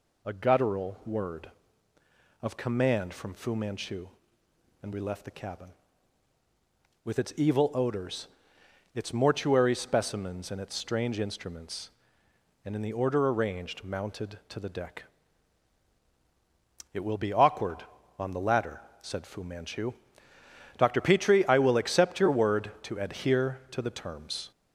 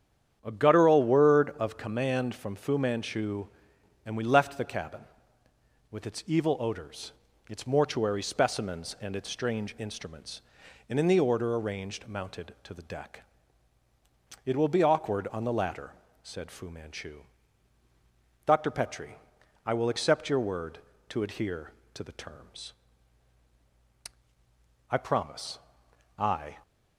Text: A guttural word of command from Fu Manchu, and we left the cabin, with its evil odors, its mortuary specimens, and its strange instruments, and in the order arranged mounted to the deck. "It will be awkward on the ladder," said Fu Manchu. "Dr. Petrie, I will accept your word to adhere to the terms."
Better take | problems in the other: first | starts louder than the rest; strong; until 1.4 s; 9 dB // goes on to say "I promise I"; from 24.9 s on; 1.6 s long

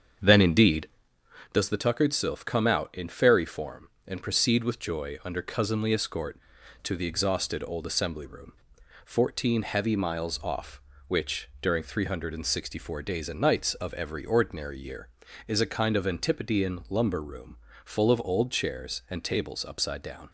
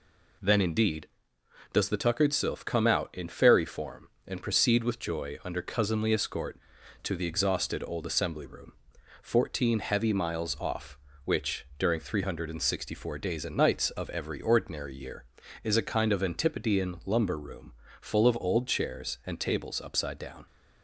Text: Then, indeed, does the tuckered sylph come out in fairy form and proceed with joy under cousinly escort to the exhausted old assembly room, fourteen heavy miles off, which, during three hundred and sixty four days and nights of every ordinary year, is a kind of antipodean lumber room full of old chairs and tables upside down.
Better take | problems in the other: second | starts louder than the rest; strong; until 1.5 s; 7.5 dB // pauses between "room" and "full"; slight; at 17.5 s; 0.28 s long; slight in the second

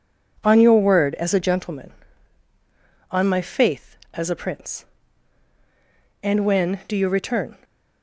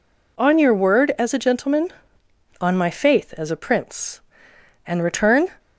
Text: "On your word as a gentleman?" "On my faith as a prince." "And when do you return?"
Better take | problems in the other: first | skips "when do you"; at 5.0 s

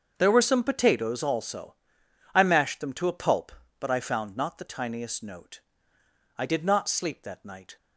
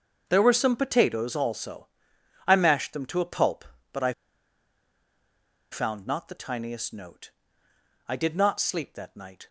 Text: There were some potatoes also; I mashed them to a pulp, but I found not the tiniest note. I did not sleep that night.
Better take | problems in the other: first | starts louder than the rest; until 1.2 s; 7 dB; also in the first // pauses between "I" and "found"; strong; at 4.1 s; 1.5 s long

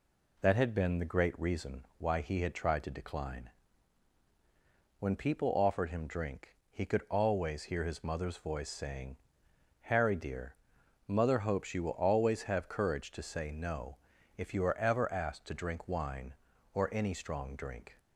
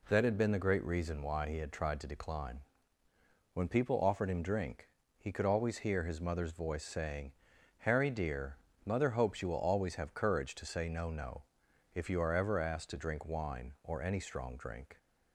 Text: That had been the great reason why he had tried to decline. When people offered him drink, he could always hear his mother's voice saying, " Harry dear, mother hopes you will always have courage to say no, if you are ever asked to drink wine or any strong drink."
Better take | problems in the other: first | says "no" twice; at 11.0 s

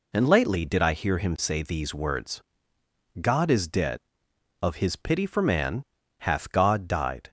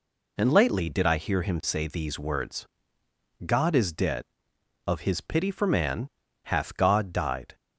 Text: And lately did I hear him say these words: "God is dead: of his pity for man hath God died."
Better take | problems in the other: neither | pauses between "man" and "hath"; the same in both

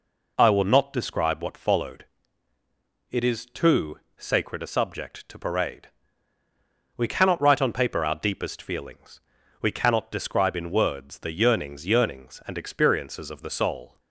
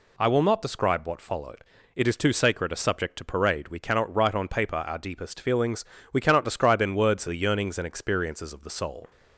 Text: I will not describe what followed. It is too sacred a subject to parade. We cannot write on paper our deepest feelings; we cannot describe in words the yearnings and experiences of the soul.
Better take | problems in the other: second | pauses between "too" and "sacred"; slight; at 3.9 s; 0.20 s long // says "yearnings" twice; at 11.8 s

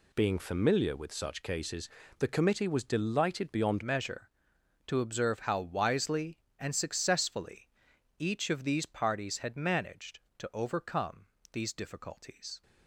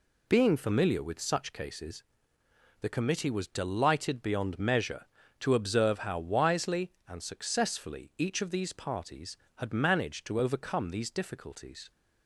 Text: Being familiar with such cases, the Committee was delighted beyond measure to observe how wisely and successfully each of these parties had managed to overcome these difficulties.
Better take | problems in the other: second | changes voice at "measure"; from 3.8 s on; 8.8 s long // pauses between "successfully" and "each"; noticeable; at 7.6 s; 0.50 s long // pauses between "overcome" and "these"; slight; at 11.2 s; 0.26 s long

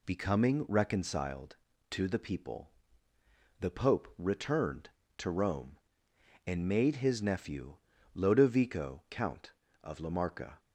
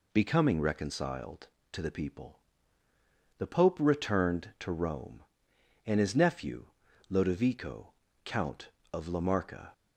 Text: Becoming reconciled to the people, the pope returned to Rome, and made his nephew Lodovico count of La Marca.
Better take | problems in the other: first | skips "made"; at 6.0 s // pauses between "nephew" and "Lodovico"; at 6.6 s; 0.42 s long; slight in the first // pauses between "Lodovico" and "count"; slight; at 7.9 s; 0.32 s long

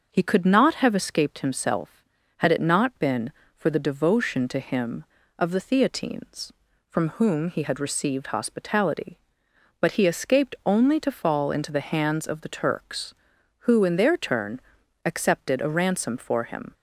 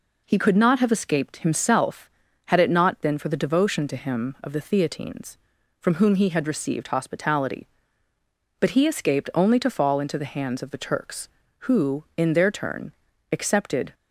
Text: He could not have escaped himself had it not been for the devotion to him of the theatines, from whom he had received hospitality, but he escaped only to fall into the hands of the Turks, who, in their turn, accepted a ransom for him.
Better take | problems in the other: first | stops before "a ransom for him"; at 13.9 s

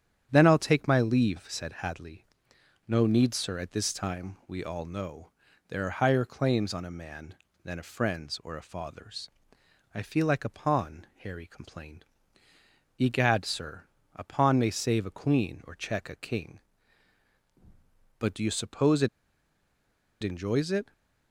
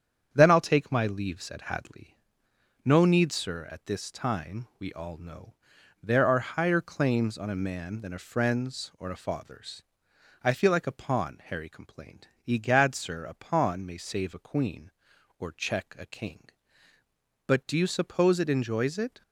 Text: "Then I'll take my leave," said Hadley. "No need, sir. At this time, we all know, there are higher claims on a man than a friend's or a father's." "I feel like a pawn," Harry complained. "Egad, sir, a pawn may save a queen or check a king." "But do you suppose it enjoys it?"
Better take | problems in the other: second | starts louder than the rest; strong; until 1.3 s; 9 dB; strong in the second // pauses between "it" and "enjoys"; at 19.0 s; 1.1 s long

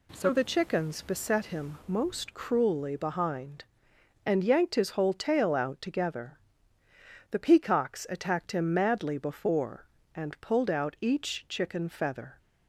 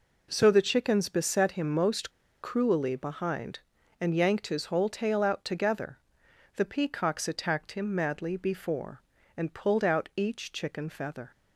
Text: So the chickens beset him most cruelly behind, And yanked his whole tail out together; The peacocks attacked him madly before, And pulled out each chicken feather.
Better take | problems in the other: first | pauses between "most" and "cruelly"; slight; at 2.1 s; 0.31 s long

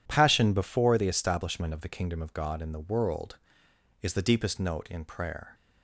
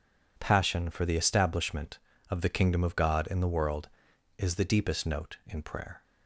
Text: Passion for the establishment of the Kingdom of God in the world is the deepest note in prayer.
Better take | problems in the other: second | says "before" for "for"; at 0.5 s

